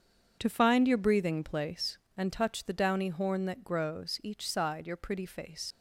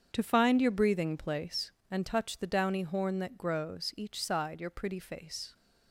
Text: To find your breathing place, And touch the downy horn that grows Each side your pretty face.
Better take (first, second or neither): second